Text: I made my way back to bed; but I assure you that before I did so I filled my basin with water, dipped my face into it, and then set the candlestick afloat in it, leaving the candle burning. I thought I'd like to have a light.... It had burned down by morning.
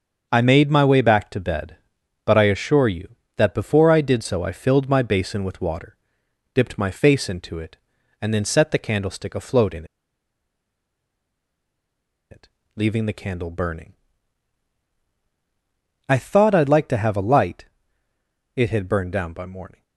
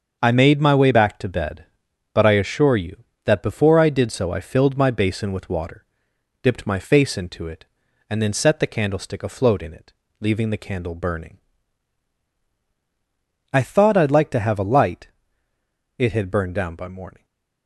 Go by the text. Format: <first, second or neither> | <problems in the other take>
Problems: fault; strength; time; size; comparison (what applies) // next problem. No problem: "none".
second | starts louder than the rest; until 1.3 s; 6.5 dB; also in the second // pauses between "in" and "it"; strong; at 9.8 s; 2.4 s long